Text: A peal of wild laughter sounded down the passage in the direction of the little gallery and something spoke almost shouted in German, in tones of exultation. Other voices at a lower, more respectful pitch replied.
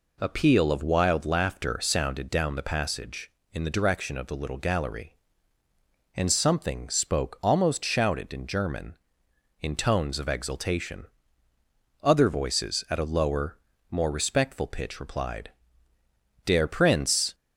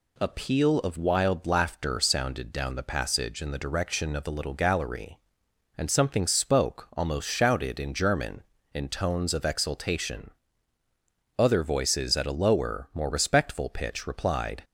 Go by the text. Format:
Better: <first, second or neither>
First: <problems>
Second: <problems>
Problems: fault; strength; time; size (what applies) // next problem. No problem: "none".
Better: second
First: goes on to say "Der Prinz"; noticeable; from 16.4 s on; 0.89 s long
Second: none